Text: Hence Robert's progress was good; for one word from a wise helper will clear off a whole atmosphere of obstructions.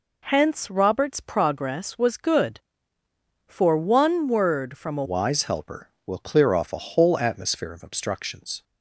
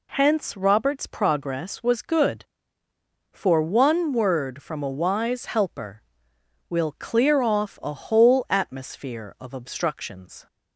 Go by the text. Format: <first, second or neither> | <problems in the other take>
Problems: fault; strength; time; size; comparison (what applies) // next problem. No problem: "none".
second | changes voice at "wise"; from 5.0 s on; 3.6 s long